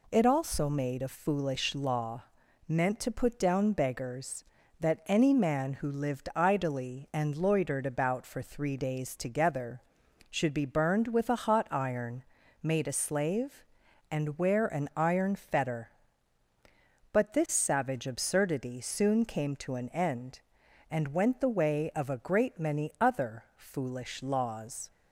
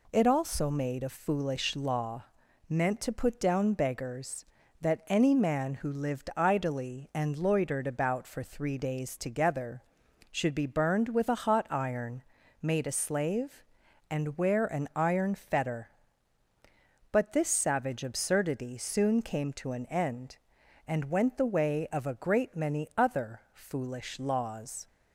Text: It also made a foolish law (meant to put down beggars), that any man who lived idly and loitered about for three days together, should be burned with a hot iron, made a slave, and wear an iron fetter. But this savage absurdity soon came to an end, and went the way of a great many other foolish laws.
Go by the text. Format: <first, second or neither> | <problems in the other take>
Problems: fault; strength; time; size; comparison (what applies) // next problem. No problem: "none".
neither | none